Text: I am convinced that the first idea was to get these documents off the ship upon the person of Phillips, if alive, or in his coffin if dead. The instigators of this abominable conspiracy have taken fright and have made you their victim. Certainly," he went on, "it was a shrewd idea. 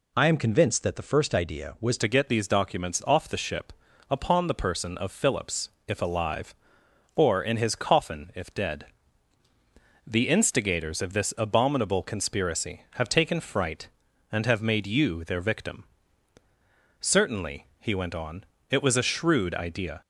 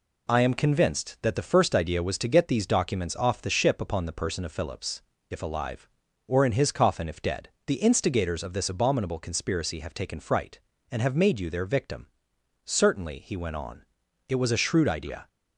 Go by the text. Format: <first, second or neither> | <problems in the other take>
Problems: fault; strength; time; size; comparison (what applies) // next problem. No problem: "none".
second | changes voice at "to"; from 1.9 s on; 18.1 s long // pauses between "ship" and "upon"; at 3.7 s; 0.38 s long